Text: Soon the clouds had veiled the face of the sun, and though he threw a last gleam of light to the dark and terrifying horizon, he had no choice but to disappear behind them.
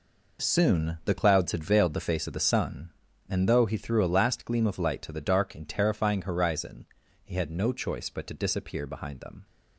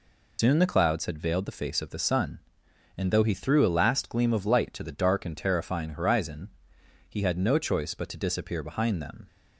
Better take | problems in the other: first | loses the start of "Soon"; at 0.3 s; 105 ms

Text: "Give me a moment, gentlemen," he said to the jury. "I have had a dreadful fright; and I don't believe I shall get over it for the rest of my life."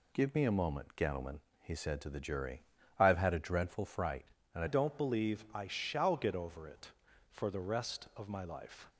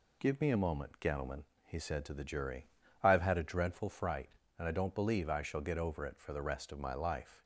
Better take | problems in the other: second | changes voice at "don't"; from 4.6 s on; 4.2 s long

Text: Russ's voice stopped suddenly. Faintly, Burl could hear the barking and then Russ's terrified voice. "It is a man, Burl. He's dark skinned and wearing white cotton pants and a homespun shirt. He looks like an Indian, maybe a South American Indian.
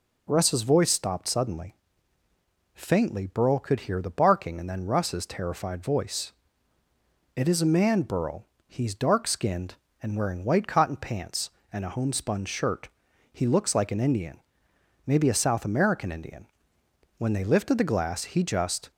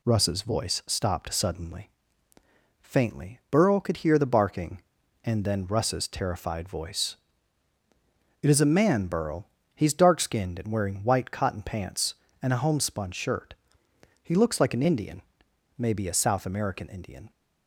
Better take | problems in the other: second | goes on to say "When they lifted the glass he just"; strong; from 17.1 s on; 1.7 s long

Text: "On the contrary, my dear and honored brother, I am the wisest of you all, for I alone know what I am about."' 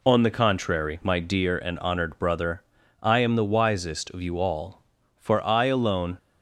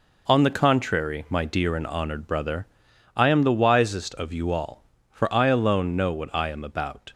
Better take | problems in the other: second | stops before "know what I am about"; at 6.1 s

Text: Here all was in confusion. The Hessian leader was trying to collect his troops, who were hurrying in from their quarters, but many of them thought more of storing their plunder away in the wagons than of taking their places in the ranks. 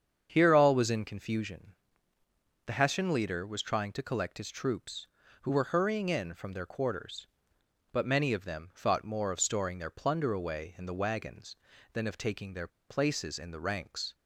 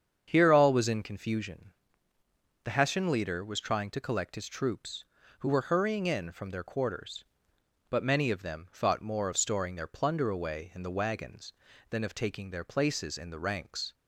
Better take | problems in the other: second | starts louder than the rest; strong; until 1.3 s; 7.5 dB; strong in the second // pauses between "their" and "places"; slight; at 12.6 s; 0.19 s long

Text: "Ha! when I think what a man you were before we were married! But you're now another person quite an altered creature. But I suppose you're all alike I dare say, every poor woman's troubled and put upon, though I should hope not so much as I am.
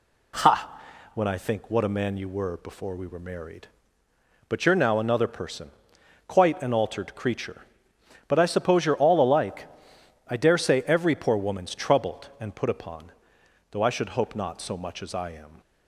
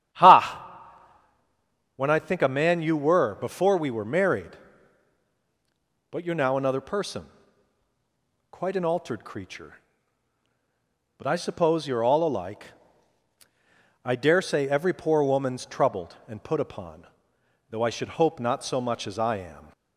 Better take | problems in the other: first | starts louder than the rest; strong; until 2.4 s; 10.5 dB // skips "what"; at 2.4 s // pauses between "person" and "quite"; at 7.2 s; 1.2 s long; noticeable in the first // pauses between "alike" and "I"; strong; at 12.6 s; 1.3 s long; noticeable in the first

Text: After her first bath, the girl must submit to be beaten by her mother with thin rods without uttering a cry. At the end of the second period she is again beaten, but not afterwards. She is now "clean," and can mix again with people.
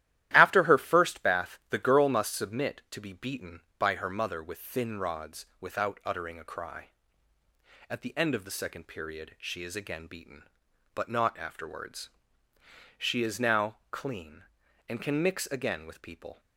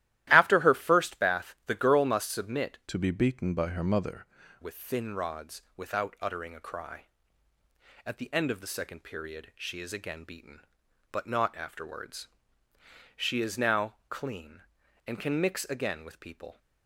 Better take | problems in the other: first | starts louder than the rest; strong; until 1.3 s; 14 dB; strong in the first // changes voice from "to" to "mother"; from 2.8 to 4.2 s; 1.4 s long // pauses between "rods" and "without"; slight; at 5.5 s; 0.16 s long; slight in the first

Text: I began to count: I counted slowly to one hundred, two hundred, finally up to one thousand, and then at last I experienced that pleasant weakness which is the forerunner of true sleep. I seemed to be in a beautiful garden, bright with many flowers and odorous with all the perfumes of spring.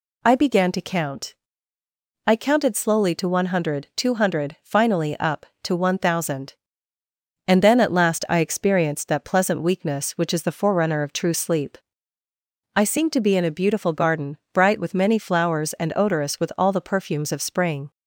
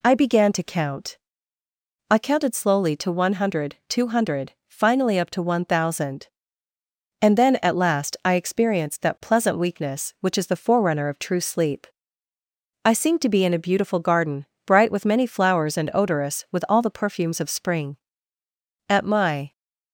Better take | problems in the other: first | goes on to say "At my"; noticeable; from 18.8 s on; 0.62 s long

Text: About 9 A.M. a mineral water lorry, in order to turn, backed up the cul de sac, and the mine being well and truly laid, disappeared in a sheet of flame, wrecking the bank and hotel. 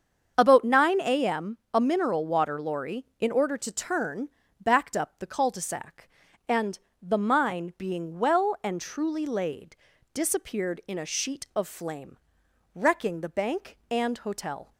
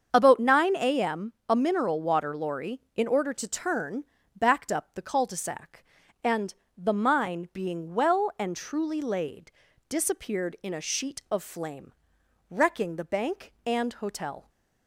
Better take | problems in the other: neither | starts louder than the rest; the same in both // pauses between "and" and "the"; slight; the same in both

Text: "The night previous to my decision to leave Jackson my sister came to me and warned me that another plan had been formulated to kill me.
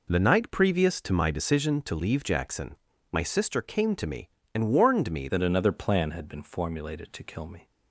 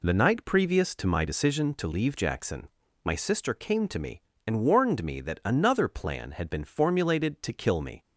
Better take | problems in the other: second | pauses between "Jackson" and "my"; slight; at 2.7 s; 0.36 s long; slight in the second // changes voice at "that"; from 5.2 s on; 2.4 s long

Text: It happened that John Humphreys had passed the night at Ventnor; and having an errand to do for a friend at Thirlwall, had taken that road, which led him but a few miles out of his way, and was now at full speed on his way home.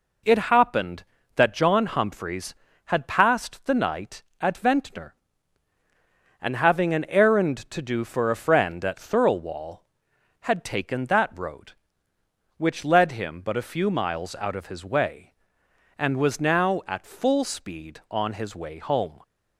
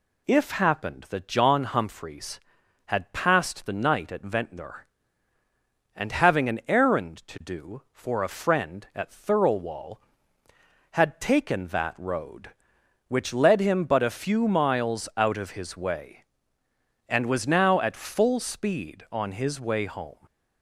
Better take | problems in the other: first | says "If" for "It"; at 0.2 s

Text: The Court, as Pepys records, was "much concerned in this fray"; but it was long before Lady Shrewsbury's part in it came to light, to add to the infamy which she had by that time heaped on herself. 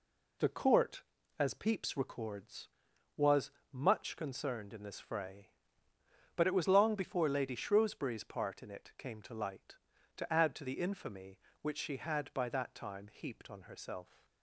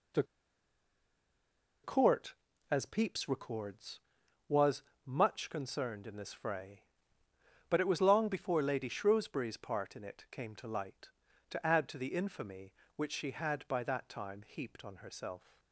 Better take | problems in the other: first | pauses between "The" and "Court"; strong; at 0.2 s; 1.5 s long // pauses between "was" and "much"; slight; at 4.8 s; 0.22 s long; slight in the first

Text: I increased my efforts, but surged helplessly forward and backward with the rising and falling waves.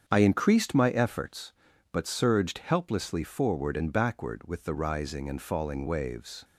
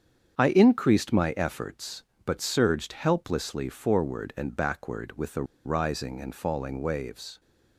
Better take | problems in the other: first | starts louder than the rest; strong; until 1.4 s; 7.5 dB; strong in the first // pauses between "the" and "rising"; slight; at 5.4 s; 0.21 s long

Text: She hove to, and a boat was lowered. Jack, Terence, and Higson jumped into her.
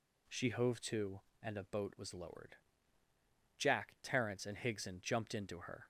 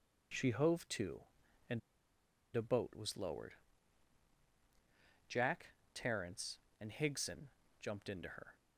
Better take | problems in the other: first | pauses between "and" and "a"; noticeable; at 1.7 s; 0.75 s long // pauses between "Higson" and "jumped"; slight; at 7.4 s; 0.30 s long

